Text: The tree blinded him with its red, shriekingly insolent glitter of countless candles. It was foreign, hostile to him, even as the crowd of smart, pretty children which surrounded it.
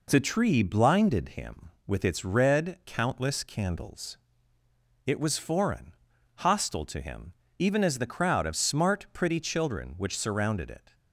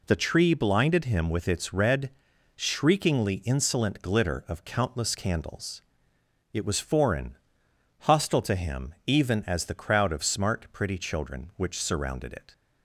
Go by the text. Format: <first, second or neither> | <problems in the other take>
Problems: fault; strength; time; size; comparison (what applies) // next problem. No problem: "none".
second | skips "shriekingly insolent glitter of"; at 2.8 s